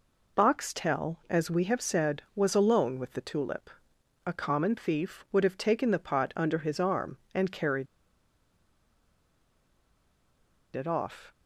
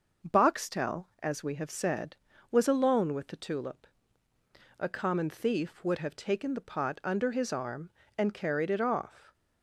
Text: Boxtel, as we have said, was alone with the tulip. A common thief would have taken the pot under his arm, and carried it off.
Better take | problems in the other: second | pauses between "carried" and "it"; strong; at 7.8 s; 2.8 s long

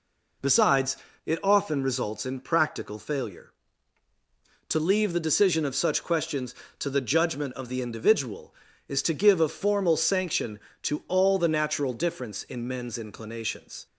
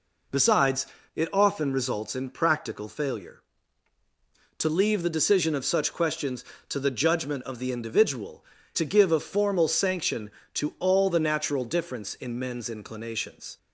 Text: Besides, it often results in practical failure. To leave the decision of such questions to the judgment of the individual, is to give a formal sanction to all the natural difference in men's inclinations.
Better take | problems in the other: first | skips "is"; at 8.5 s

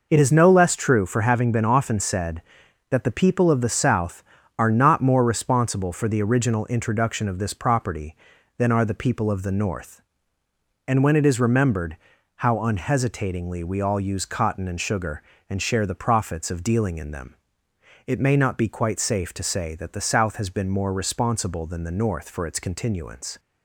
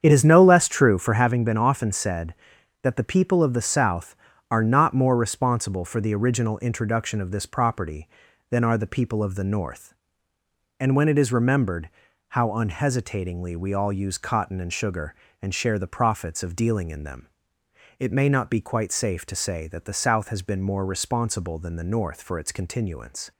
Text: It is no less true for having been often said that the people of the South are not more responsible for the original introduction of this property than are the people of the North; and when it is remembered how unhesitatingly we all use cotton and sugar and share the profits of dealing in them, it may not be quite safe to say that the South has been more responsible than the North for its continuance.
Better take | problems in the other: first | starts louder than the rest; strong; until 1.4 s; 8 dB // pauses between "remembered" and "how"; at 11.8 s; 0.38 s long; also in the first

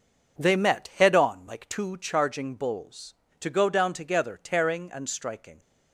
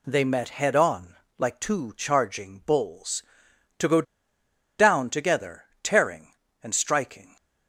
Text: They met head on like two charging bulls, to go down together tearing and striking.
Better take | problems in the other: first | pauses between "on" and "like"; slight; at 1.1 s; 0.22 s long // pauses between "go" and "down"; noticeable; at 4.0 s; 0.76 s long // pauses between "together" and "tearing"; slight; at 5.6 s; 0.18 s long

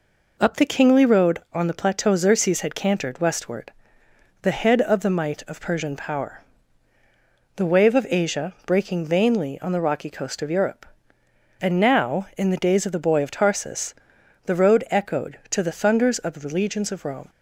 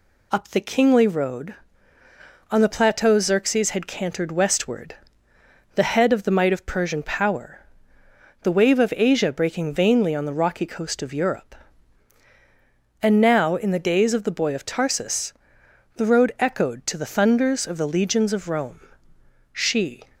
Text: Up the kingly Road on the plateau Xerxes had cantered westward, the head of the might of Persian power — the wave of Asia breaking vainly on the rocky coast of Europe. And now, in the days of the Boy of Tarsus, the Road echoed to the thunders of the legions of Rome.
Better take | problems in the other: first | goes on to say "She"; from 19.5 s on; 0.50 s long

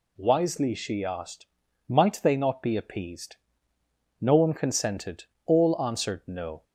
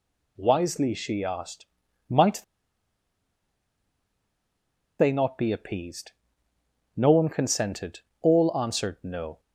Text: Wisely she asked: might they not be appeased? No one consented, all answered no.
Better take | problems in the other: first | pauses between "might" and "they"; strong; at 2.4 s; 2.5 s long

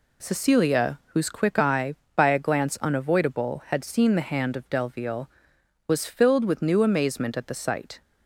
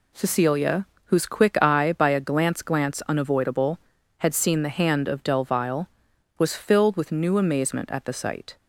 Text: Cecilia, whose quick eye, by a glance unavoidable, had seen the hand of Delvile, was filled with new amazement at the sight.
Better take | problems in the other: first | says "glance" twice; at 2.6 s

